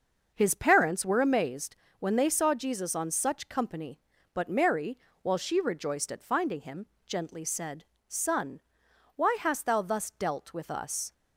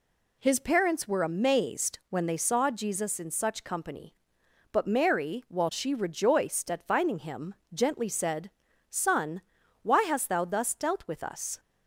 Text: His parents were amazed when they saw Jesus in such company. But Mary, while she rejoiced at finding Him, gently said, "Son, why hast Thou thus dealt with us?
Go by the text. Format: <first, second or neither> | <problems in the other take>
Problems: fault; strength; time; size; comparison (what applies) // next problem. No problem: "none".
second | starts louder than the rest; noticeable; until 1.3 s; 6 dB // pauses between "amazed" and "when"; slight; at 1.7 s; 0.22 s long // says "on" for "in"; at 2.9 s